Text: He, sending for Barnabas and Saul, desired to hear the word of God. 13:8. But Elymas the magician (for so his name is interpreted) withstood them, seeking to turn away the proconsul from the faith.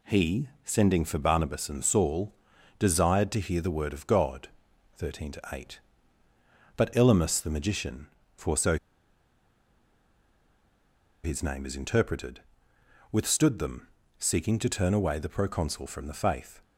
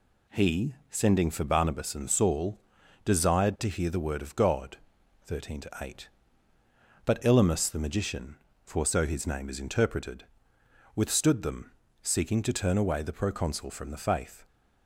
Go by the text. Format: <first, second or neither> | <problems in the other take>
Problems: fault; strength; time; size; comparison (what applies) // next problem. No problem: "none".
second | pauses between "so" and "his"; strong; at 8.7 s; 2.4 s long